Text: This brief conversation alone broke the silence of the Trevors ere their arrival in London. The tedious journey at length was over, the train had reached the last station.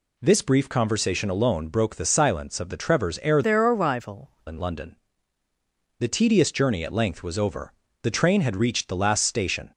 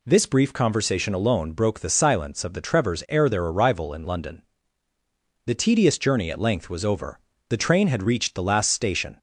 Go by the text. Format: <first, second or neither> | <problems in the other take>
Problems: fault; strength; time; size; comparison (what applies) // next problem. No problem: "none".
second | changes voice from "their" to "arrival"; from 3.4 to 4.3 s; 0.9 s long